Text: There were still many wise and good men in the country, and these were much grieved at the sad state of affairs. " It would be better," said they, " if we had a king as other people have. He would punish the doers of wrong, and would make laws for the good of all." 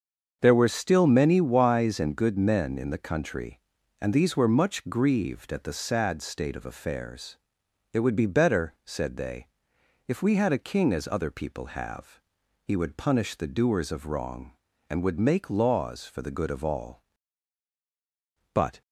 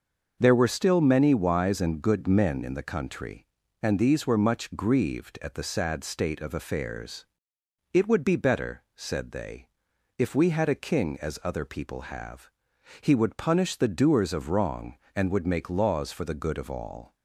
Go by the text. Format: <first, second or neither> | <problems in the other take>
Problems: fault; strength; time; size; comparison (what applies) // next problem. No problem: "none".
second | starts louder than the rest; until 1.4 s; 6.5 dB; also in the second // goes on to say "But"; slight; from 18.5 s on; 0.28 s long